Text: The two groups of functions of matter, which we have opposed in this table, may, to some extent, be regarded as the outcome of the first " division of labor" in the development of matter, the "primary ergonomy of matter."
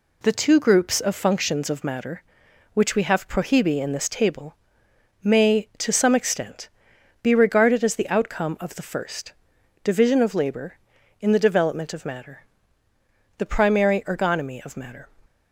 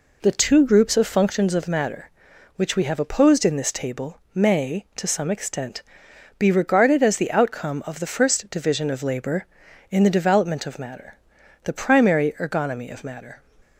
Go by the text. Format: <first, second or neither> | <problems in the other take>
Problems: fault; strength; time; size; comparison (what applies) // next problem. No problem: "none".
second | says "prohibi" for "opposed"; at 3.2 s